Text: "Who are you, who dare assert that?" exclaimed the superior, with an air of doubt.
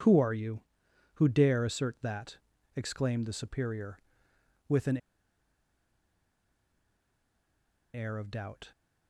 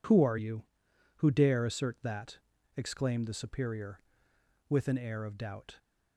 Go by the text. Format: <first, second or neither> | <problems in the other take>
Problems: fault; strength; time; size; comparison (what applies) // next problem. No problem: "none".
second | pauses between "an" and "air"; strong; at 4.9 s; 2.9 s long